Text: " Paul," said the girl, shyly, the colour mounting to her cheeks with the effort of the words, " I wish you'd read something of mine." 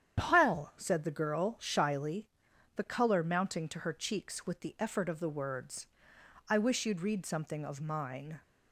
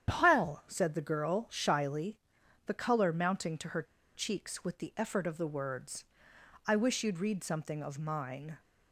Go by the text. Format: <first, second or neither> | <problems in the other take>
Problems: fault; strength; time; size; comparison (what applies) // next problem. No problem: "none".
first | starts louder than the rest; strong; until 1.1 s; 9 dB; strong in the first // pauses between "her" and "cheeks"; slight; at 3.8 s; 0.31 s long